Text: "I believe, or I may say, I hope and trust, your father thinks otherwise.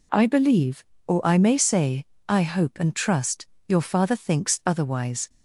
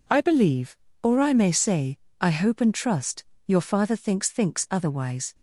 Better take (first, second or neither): first